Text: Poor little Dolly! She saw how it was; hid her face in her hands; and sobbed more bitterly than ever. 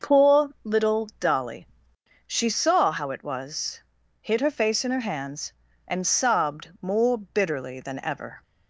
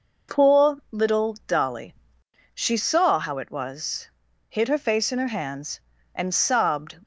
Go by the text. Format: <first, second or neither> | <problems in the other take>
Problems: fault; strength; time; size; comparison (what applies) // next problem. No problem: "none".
first | stops before "more bitterly than ever"; at 7.0 s